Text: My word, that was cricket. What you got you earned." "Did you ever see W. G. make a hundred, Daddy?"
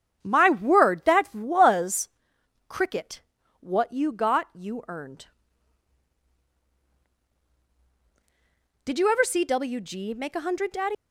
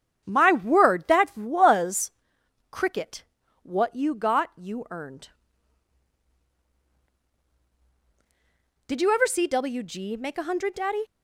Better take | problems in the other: second | starts louder than the rest; strong; until 1.2 s; 8.5 dB; strong in the second // pauses between "was" and "cricket"; noticeable; at 2.0 s; 0.58 s long; noticeable in the second // leaves "Daddy" unfinished; at 10.9 s; 75 ms

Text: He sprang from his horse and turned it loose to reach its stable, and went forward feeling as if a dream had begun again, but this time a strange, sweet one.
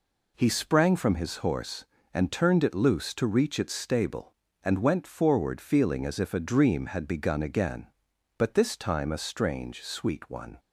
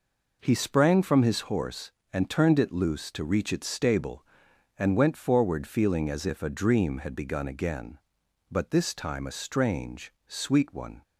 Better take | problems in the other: neither | none

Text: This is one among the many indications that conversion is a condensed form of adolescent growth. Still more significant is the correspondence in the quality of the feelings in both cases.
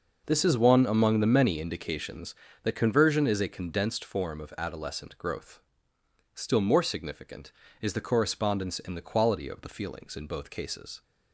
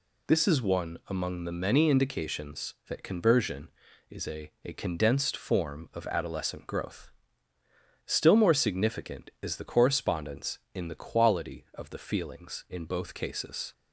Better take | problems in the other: first | says "a" twice; at 4.6 s

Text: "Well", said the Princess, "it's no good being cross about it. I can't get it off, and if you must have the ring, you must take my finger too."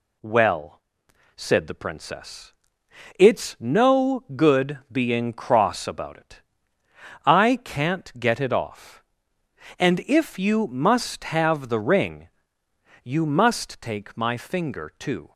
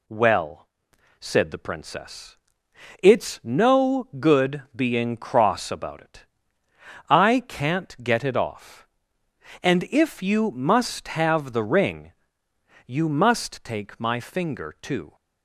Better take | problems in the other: neither | none

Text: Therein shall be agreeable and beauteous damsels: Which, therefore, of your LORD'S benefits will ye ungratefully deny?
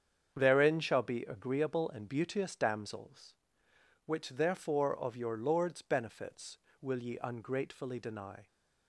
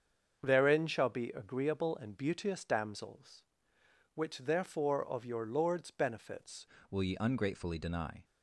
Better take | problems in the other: first | starts louder than the rest; until 1.4 s; 7 dB; strong in the first // changes voice at "will"; from 6.9 s on; 1.3 s long

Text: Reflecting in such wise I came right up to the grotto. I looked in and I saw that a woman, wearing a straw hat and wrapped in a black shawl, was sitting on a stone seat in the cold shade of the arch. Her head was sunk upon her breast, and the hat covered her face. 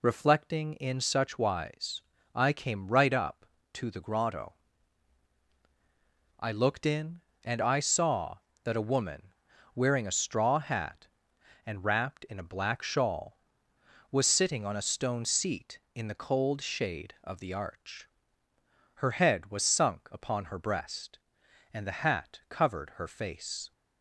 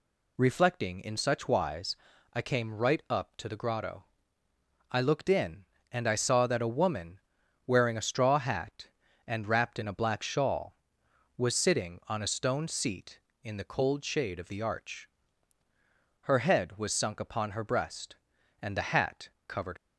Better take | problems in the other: first | pauses between "wise" and "I"; at 1.9 s; 0.38 s long; slight in the first // pauses between "hat" and "covered"; slight; at 19.2 s; 0.18 s long // stops before "her face"; at 19.7 s

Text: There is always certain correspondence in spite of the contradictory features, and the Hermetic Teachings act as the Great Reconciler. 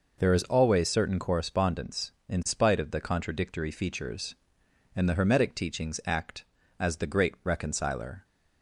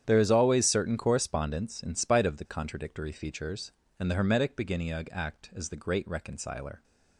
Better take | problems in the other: first | starts louder than the rest; strong; until 1.0 s; 9.5 dB // says "Beginniug" for "Teachings"; at 4.5 s

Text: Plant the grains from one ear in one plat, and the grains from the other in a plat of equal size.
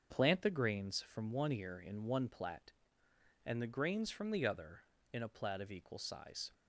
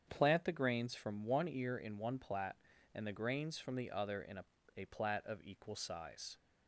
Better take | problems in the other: first | starts louder than the rest; strong; until 1.1 s; 8 dB; also in the first // says "a" twice; at 4.7 s

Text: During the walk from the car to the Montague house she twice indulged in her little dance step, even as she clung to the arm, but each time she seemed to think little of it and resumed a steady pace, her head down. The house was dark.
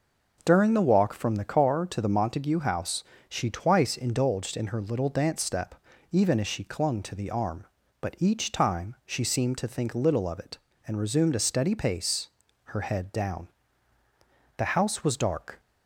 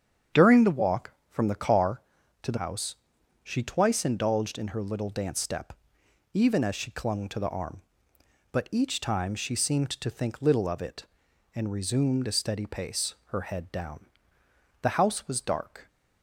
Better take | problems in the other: first | starts louder than the rest; strong; until 1.5 s; 8 dB // skips "Montague"; at 2.5 s // pauses between "house" and "she"; noticeable; at 2.9 s; 0.48 s long; slight in the first

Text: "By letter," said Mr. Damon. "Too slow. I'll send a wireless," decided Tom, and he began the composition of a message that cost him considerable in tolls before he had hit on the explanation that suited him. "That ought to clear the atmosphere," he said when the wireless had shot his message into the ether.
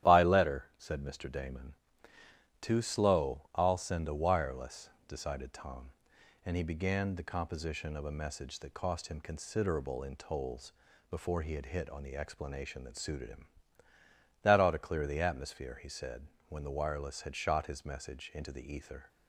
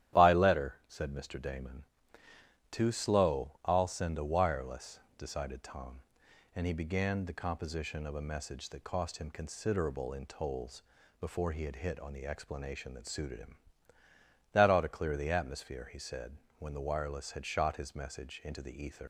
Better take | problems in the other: first | starts louder than the rest; strong; until 1.2 s; 11.5 dB; strong in the first // pauses between "tolls" and "before"; slight; at 10.8 s; 0.34 s long; slight in the first // pauses between "said" and "when"; slight; at 16.3 s; 0.24 s long; slight in the first // leaves "ether" unfinished; at 19.0 s; 105 ms

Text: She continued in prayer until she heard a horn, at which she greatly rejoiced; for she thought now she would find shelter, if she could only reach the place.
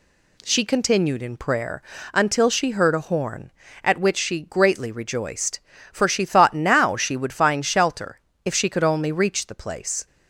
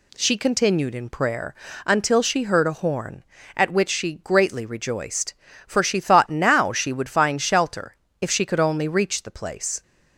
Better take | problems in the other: neither | pauses between "prayer" and "until"; slight; the same in both

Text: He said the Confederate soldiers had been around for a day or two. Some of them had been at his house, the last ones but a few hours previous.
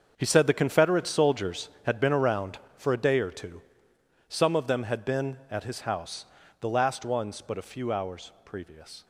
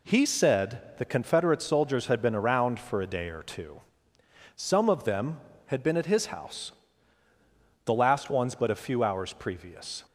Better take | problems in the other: second | gets quieter; strong; throughout; 11.5 dB

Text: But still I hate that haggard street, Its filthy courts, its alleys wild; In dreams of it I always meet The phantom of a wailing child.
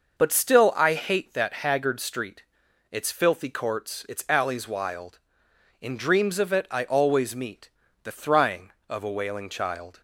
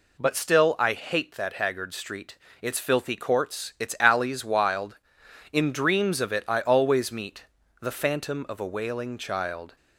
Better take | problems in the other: second | pauses between "meet" and "The"; slight; at 7.6 s; 0.34 s long; slight in the second // says "thrying" for "phantom"; at 8.1 s

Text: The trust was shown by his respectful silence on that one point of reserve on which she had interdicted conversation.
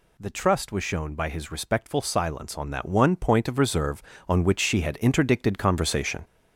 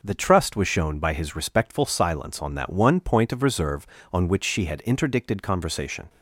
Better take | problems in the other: second | gets louder; noticeable; throughout; 5.5 dB

